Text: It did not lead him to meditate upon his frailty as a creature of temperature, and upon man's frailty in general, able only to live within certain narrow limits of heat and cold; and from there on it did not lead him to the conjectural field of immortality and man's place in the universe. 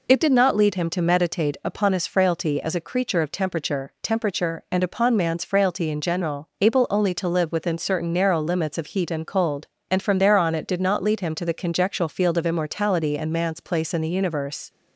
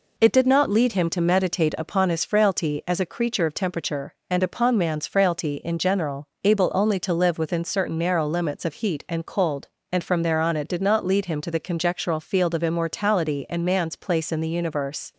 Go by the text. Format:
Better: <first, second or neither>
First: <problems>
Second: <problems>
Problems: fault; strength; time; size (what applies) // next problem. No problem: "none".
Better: second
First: says "temperature" twice; at 4.0 s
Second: none